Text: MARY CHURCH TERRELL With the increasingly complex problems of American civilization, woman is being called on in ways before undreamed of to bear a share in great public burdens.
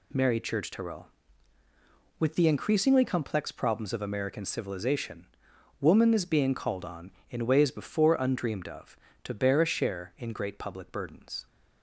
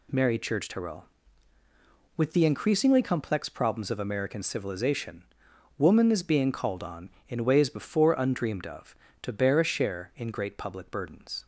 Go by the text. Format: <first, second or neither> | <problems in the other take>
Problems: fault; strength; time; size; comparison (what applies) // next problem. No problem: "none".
neither | none